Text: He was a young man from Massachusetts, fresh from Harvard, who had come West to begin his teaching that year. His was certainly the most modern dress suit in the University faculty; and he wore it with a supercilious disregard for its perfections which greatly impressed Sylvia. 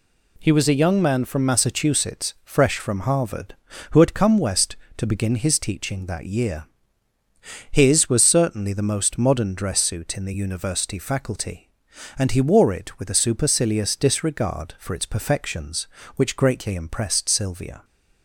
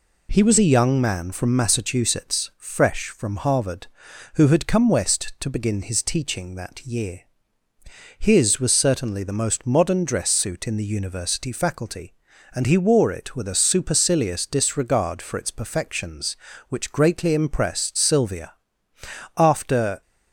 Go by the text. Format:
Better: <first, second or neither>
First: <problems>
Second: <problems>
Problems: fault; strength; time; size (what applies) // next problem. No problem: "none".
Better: first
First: none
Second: goes on to say "After"; noticeable; from 19.3 s on; 0.66 s long